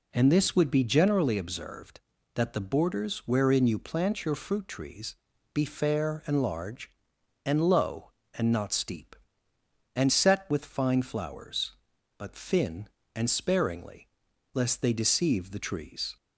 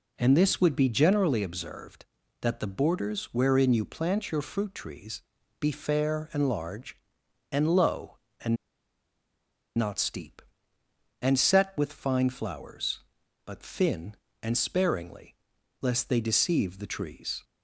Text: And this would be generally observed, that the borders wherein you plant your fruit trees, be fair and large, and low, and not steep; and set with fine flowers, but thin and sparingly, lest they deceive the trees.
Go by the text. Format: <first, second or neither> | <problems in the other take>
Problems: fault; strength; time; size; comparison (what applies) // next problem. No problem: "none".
first | pauses between "and" and "not"; at 8.5 s; 1.2 s long